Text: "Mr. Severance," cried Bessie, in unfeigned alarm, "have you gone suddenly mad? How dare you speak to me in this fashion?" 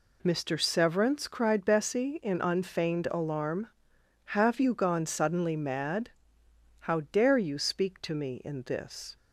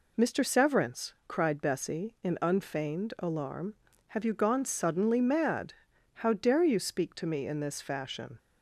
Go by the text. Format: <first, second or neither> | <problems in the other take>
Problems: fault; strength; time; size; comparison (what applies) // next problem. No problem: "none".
second | stops before "fashion"; at 9.1 s